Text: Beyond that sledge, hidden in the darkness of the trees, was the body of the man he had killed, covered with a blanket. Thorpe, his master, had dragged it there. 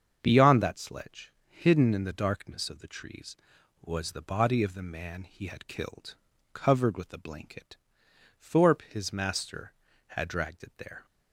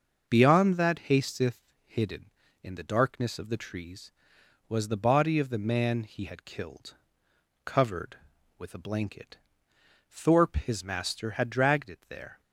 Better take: first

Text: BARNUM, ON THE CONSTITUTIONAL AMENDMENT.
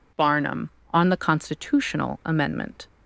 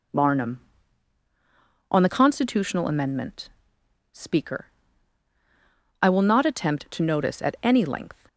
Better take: first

